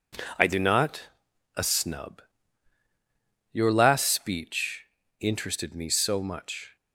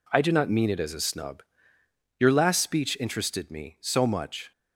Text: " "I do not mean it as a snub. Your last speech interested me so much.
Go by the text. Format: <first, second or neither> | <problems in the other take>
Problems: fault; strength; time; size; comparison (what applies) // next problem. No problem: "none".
second | skips "mean it as"; at 1.3 s // pauses between "speech" and "interested"; slight; at 4.8 s; 0.34 s long